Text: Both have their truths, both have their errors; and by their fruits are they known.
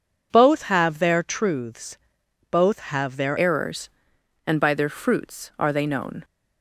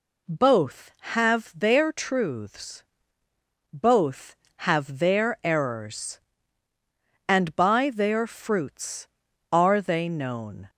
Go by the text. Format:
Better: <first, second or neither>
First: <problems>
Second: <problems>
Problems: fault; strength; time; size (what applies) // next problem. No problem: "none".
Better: second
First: changes voice at "errors"; from 3.3 s on; 2.9 s long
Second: none